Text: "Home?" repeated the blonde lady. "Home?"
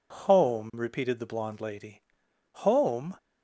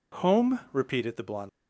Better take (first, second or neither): first